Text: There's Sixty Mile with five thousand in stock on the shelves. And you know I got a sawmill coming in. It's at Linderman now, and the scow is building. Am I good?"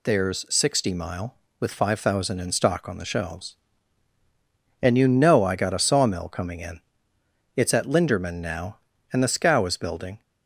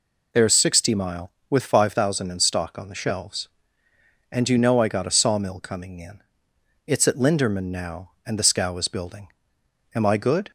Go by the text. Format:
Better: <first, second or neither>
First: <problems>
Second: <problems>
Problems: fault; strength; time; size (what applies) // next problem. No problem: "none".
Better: second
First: stops before "Am I good"; at 10.2 s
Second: none